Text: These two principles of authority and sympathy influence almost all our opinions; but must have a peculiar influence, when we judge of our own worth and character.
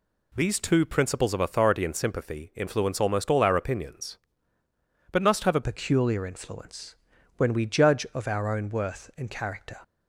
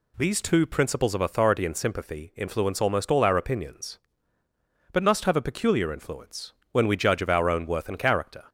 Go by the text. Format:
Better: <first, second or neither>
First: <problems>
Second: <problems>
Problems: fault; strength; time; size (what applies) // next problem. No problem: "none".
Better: second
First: changes voice at "peculiar"; from 5.6 s on; 4.2 s long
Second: none